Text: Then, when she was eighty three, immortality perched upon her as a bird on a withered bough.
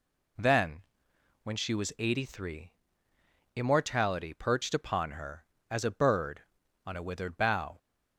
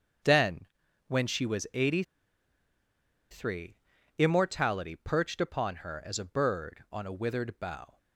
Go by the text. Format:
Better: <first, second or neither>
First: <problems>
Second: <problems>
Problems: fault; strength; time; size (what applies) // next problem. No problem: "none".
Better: first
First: none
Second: starts louder than the rest; strong; until 1.6 s; 7.5 dB // pauses between "eighty" and "three"; strong; at 2.0 s; 1.2 s long